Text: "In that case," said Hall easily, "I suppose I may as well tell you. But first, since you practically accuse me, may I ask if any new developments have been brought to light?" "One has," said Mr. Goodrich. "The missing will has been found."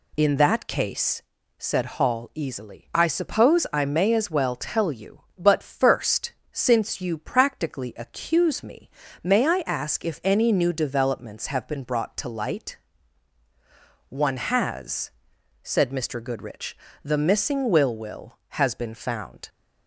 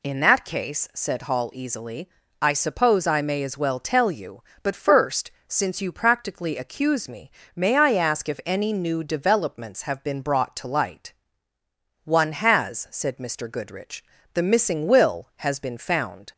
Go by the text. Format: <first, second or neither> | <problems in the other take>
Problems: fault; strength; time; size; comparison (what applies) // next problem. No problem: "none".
second | says "will" twice; at 17.9 s